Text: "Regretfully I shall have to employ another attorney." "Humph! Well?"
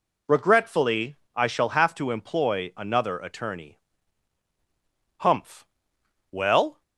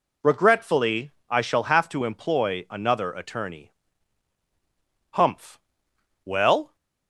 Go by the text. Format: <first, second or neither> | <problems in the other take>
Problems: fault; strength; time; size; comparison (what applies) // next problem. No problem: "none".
neither | pauses between "Regretfully" and "I"; slight; the same in both